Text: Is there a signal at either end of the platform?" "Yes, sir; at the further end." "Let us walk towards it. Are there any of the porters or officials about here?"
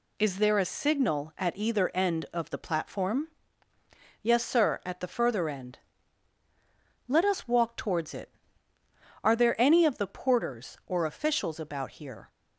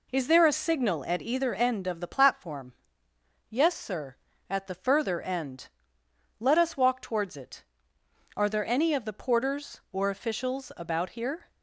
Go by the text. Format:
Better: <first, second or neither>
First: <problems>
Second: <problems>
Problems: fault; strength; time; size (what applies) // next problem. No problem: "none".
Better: neither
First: none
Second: none